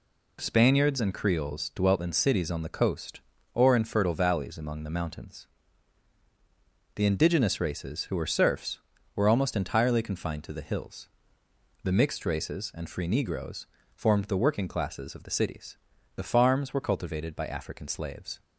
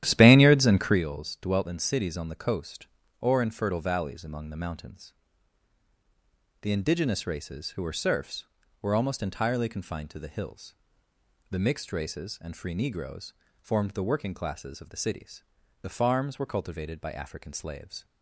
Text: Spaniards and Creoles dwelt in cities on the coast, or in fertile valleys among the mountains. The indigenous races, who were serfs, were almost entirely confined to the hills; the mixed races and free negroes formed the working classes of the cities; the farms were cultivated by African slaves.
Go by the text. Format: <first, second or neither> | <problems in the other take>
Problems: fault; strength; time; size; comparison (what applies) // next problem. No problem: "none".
first | starts louder than the rest; strong; until 1.0 s; 12 dB // pauses between "negroes" and "formed"; slight; at 13.3 s; 0.29 s long; slight in the first